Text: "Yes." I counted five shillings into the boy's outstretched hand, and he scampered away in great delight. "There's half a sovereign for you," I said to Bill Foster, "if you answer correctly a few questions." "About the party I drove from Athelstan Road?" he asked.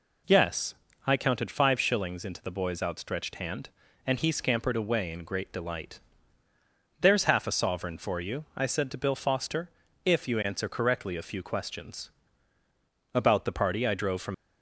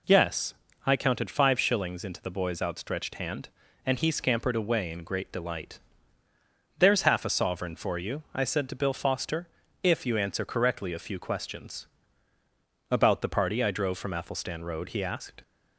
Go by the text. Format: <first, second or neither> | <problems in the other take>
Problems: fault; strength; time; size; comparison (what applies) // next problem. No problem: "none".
second | stops before "Athelstan Road he asked"; at 14.3 s